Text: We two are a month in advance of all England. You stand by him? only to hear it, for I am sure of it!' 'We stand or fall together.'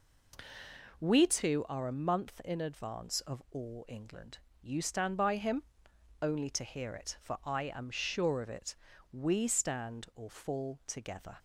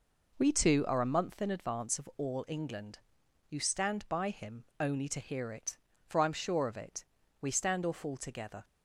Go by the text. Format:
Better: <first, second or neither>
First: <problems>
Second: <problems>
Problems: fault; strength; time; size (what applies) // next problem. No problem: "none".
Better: neither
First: none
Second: none